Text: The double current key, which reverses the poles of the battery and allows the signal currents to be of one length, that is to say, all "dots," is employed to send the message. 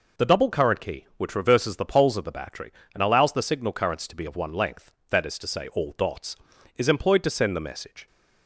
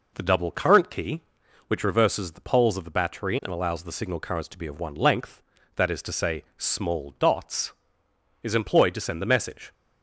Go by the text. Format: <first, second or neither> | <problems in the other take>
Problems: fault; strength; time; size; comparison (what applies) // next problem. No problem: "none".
first | says "small" for "all"; at 6.5 s